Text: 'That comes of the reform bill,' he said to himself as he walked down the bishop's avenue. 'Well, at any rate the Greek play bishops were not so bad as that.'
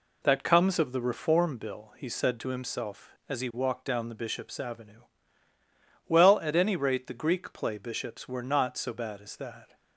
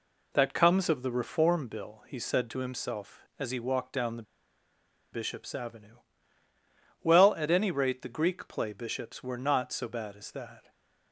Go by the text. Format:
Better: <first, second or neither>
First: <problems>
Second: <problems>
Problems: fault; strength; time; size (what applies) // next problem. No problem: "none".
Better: first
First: none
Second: pauses between "the" and "bishop's"; noticeable; at 4.2 s; 0.90 s long // stays silent after the last word; slight; from 10.6 s on; 0.5 s long